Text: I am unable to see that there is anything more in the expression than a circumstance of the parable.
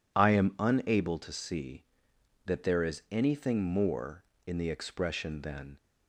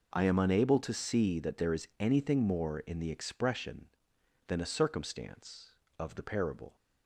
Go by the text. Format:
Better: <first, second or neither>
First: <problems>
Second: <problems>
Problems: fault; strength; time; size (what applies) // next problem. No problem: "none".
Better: second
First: stops before "a circumstance of the parable"; at 5.7 s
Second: none